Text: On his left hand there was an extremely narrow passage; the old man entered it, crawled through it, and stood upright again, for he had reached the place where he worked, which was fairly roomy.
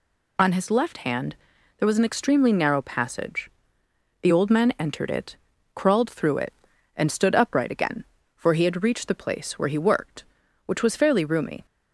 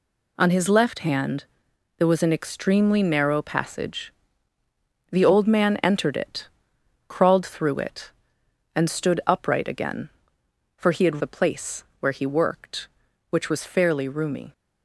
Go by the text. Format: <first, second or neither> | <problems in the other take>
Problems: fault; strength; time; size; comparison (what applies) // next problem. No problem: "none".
first | pauses between "hand" and "there"; noticeable; at 1.4 s; 0.52 s long; also in the first // skips "reached"; at 11.2 s // pauses between "place" and "where"; slight; at 11.8 s; 0.16 s long